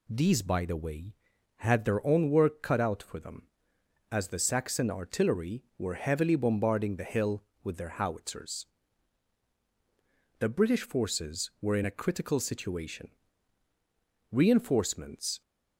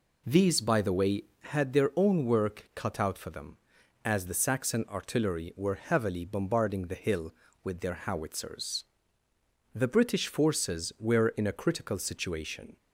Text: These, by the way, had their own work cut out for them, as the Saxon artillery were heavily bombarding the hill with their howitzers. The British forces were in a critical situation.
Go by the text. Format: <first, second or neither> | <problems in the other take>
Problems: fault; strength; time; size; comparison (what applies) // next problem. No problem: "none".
second | goes on to say "Reinforcements"; noticeable; from 14.3 s on; 1.1 s long